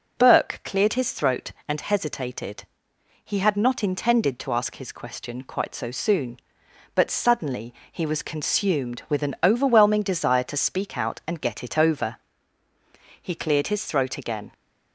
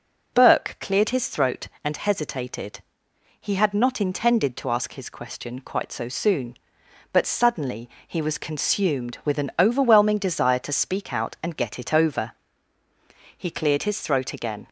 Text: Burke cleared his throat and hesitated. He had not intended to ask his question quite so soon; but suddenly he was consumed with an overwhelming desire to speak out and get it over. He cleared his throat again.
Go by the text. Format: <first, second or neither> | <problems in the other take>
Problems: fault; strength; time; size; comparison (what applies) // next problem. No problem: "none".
neither | pauses between "suddenly" and "he"; slight; the same in both